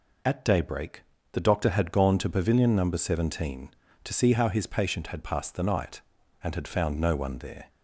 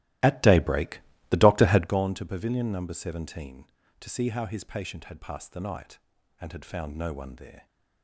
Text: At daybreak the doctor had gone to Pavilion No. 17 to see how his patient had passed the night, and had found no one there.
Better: first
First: pauses between "daybreak" and "the"; slight; at 1.0 s; 0.28 s long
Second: starts louder than the rest; strong; until 2.0 s; 16 dB // pauses between "daybreak" and "the"; slight; at 1.0 s; 0.28 s long

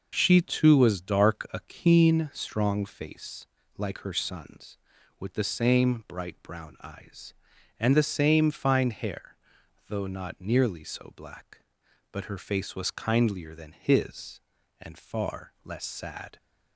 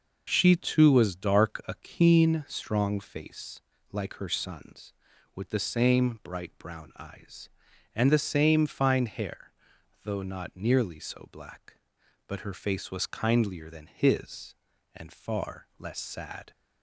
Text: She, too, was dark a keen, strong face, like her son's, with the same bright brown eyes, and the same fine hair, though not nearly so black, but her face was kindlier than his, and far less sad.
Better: neither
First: none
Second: none

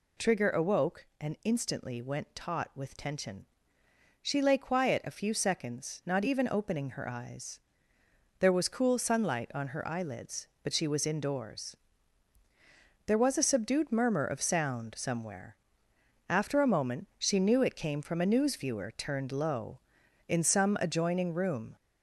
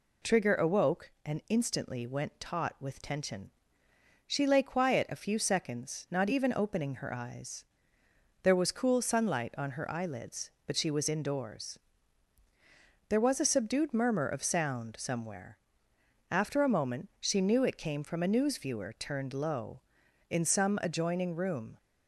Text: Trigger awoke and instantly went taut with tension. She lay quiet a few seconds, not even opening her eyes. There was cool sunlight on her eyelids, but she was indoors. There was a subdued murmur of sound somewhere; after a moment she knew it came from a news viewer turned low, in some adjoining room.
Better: second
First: gets louder; noticeable; throughout; 4.5 dB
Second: none

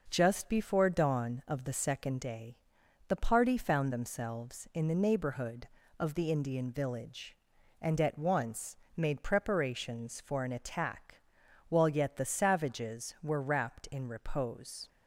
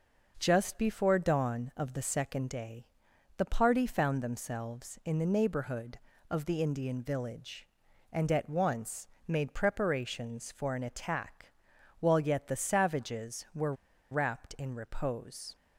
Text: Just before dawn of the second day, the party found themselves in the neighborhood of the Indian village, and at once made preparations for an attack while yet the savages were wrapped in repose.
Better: first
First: pauses between "once" and "made"; slight; at 8.7 s; 0.18 s long // pauses between "attack" and "while"; noticeable; at 11.2 s; 0.48 s long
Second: pauses between "once" and "made"; slight; at 9.0 s; 0.18 s long // pauses between "attack" and "while"; noticeable; at 11.5 s; 0.48 s long // pauses between "were" and "wrapped"; at 13.7 s; 0.37 s long

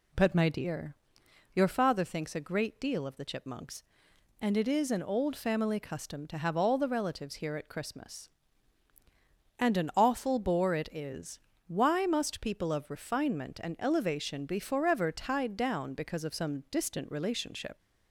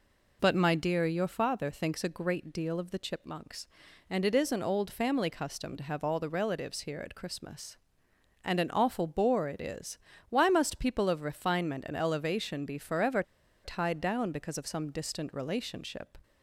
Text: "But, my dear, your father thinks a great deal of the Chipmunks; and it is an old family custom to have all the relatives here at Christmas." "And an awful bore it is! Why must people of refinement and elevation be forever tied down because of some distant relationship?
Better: first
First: none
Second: pauses between "forever" and "tied"; at 13.2 s; 0.41 s long

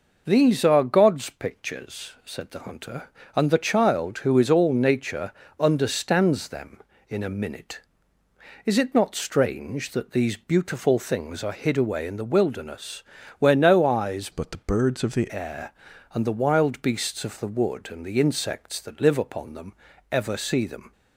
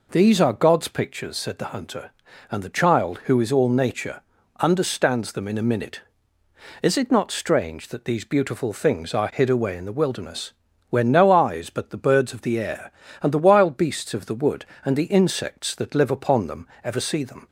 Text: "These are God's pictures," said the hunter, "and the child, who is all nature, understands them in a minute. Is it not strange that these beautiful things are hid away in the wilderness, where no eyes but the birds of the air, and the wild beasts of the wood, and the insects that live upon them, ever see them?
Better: second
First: changes voice from "but" to "the"; from 14.3 to 15.3 s; 1.0 s long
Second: none

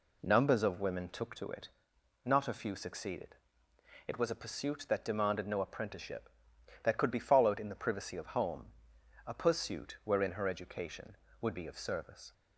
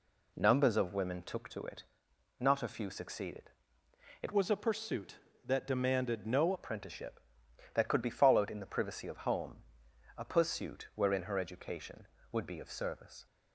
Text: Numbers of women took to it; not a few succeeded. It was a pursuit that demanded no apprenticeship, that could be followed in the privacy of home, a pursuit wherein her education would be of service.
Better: first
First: none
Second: changes voice from "was" to "no"; from 4.3 to 6.5 s; 2.2 s long

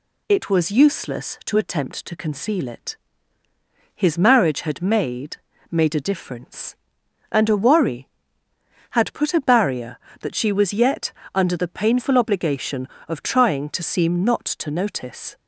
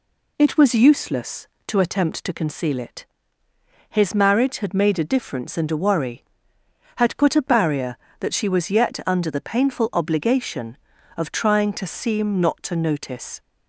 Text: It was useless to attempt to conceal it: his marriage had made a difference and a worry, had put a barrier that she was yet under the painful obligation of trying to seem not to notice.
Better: second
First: says "made" twice; at 5.7 s // pauses between "yet" and "under"; slight; at 11.1 s; 0.22 s long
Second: none

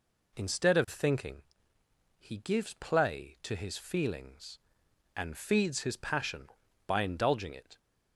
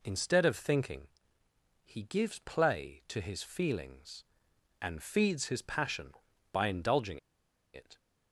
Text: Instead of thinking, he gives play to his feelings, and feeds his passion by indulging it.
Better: first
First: none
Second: pauses between "indulging" and "it"; noticeable; at 7.1 s; 0.55 s long

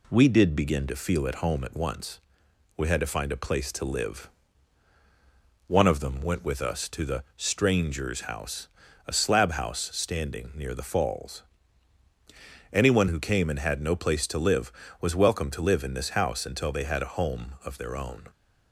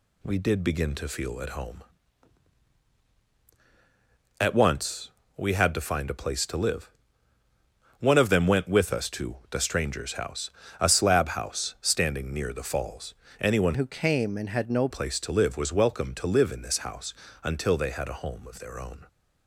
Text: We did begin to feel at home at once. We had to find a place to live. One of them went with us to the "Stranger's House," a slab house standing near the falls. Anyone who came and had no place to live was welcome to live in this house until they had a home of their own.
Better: first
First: none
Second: changes voice from "who" to "no"; from 13.7 to 14.8 s; 1.1 s long // pauses between "house" and "until"; slight; at 17.1 s; 0.30 s long

